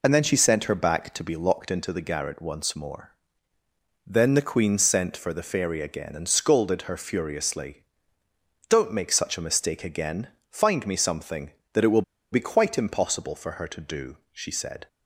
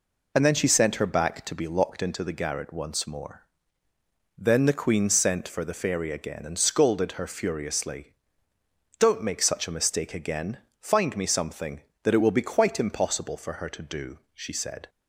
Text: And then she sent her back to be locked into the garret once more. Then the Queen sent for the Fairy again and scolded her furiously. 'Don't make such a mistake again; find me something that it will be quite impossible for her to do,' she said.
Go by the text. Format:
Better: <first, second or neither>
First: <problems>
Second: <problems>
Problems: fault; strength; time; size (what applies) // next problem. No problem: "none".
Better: second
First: pauses between "will" and "be"; slight; at 12.0 s; 0.30 s long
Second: none